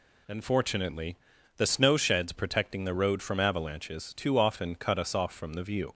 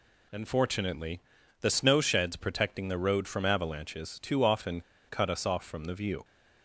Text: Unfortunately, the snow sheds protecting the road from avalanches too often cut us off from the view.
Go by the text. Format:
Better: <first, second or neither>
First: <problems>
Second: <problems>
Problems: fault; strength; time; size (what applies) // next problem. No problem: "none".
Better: first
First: none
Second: pauses between "often" and "cut"; slight; at 4.8 s; 0.27 s long